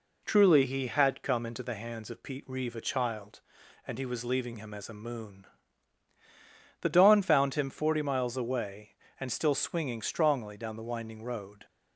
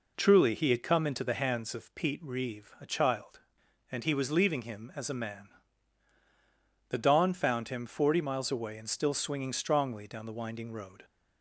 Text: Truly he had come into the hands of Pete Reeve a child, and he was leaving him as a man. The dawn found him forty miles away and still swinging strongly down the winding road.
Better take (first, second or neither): second